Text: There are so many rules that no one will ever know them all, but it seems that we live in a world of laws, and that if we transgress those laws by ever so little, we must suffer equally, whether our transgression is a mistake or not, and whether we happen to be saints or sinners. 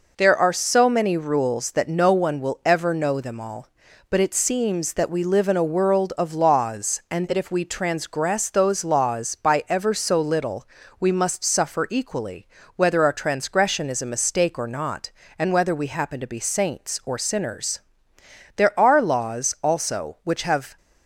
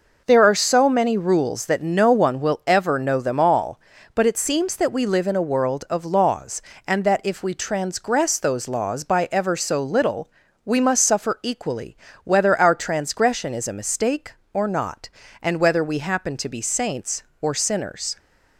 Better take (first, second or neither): second